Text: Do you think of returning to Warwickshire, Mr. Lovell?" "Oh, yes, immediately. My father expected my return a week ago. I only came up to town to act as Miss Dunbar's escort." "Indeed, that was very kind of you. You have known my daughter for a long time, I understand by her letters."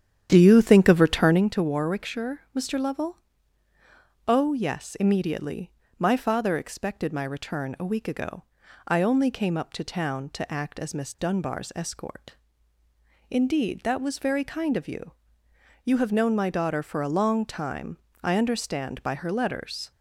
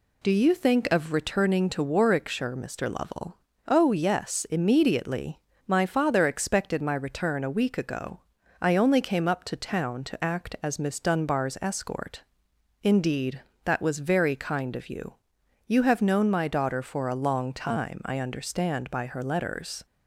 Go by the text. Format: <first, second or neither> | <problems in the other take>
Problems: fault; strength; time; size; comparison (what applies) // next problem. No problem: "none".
second | starts louder than the rest; strong; until 1.6 s; 9.5 dB